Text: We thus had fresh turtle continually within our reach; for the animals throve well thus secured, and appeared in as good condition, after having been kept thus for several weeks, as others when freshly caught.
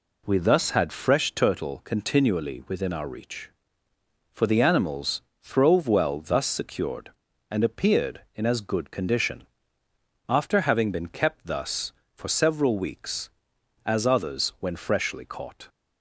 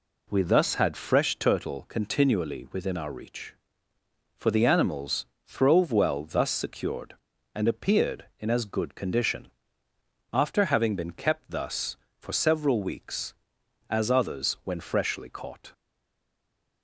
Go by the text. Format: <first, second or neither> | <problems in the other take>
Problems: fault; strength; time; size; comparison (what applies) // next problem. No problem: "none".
first | pauses between "animals" and "throve"; slight; at 5.2 s; 0.22 s long; slight in the first // stays silent after the last word; from 15.7 s on; 1.1 s long